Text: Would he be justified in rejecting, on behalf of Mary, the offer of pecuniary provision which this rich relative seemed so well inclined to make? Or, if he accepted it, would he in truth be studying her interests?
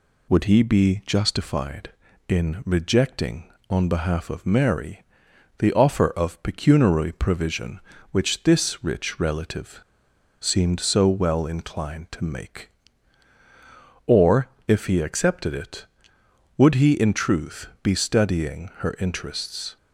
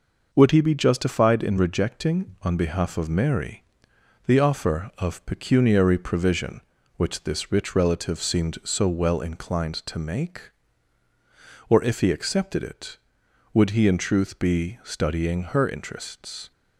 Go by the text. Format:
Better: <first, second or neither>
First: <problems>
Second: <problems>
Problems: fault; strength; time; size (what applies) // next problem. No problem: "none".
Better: second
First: pauses between "relative" and "seemed"; noticeable; at 9.7 s; 0.61 s long // pauses between "truth" and "be"; slight; at 17.6 s; 0.16 s long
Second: none